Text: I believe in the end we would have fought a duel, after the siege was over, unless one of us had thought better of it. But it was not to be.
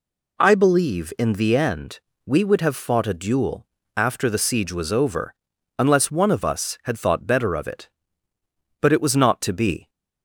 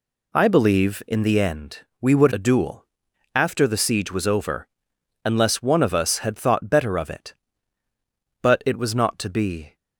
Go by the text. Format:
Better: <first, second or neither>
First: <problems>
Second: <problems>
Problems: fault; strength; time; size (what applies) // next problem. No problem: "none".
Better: first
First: pauses between "end" and "we"; slight; at 2.0 s; 0.24 s long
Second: pauses between "end" and "we"; slight; at 1.7 s; 0.20 s long // skips "have fought"; at 2.3 s